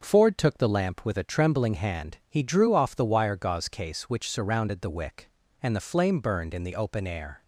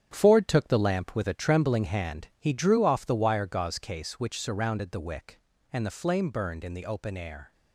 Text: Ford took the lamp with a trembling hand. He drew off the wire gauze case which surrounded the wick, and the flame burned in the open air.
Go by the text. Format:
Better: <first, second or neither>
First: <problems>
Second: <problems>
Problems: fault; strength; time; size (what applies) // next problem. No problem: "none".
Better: first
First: none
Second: gets quieter; strong; throughout; 9 dB